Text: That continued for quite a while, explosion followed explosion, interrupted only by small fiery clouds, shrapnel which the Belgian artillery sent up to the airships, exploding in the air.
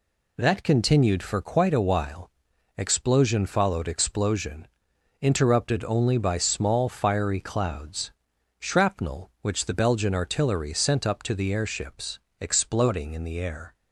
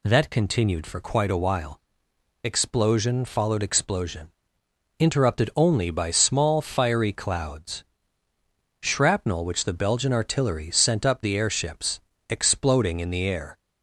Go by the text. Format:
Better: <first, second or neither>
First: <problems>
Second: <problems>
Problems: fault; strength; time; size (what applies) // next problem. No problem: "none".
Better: first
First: none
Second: skips "to"; at 11.2 s